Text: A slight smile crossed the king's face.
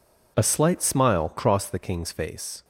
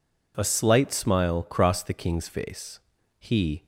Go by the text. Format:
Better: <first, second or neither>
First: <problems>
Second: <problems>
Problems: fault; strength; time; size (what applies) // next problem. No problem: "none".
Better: first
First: none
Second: goes on to say "He"; slight; from 3.1 s on; 0.48 s long